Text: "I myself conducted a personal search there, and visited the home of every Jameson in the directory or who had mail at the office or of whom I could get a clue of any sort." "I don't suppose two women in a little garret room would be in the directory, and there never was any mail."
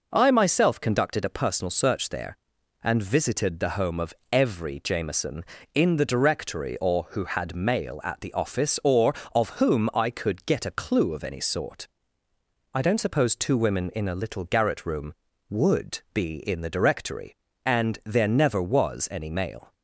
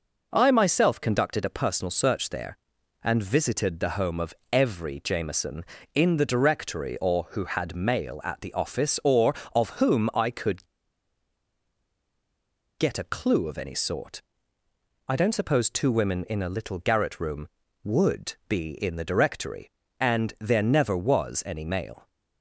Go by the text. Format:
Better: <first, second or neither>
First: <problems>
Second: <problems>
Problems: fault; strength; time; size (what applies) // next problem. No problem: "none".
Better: first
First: pauses between "of" and "every"; slight; at 4.1 s; 0.18 s long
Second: pauses between "of" and "every"; slight; at 4.3 s; 0.18 s long // pauses between "could" and "get"; strong; at 10.6 s; 2.1 s long